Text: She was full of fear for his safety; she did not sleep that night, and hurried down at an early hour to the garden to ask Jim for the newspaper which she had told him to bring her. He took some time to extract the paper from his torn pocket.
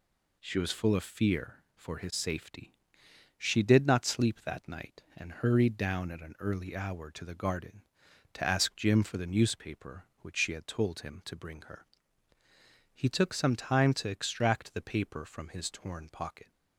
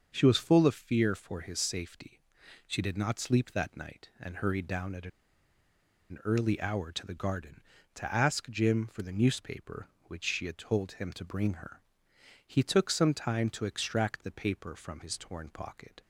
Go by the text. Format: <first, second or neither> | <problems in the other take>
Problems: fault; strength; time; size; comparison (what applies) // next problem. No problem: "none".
first | starts louder than the rest; until 1.1 s; 6.5 dB // pauses between "at" and "an"; at 5.0 s; 1.0 s long